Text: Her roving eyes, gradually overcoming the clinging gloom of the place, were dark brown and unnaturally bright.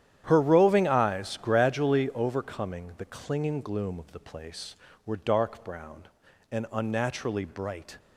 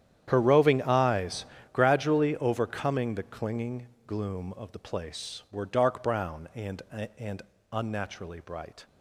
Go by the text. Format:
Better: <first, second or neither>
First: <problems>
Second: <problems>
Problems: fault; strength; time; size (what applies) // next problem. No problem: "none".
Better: first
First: starts louder than the rest; strong; until 1.2 s; 10.5 dB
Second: starts louder than the rest; strong; until 1.2 s; 10 dB // pauses between "clinging" and "gloom"; slight; at 3.8 s; 0.18 s long // says "and" twice; at 7.1 s